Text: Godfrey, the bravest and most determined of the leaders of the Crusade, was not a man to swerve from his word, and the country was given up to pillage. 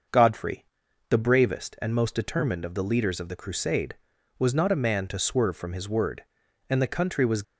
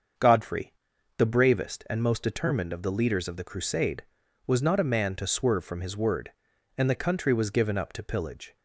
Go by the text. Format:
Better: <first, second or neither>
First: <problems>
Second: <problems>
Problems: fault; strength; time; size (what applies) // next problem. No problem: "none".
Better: second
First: starts louder than the rest; noticeable; until 1.5 s; 6 dB // stops before "given up to pillage"; at 7.4 s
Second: starts louder than the rest; until 1.6 s; 6.5 dB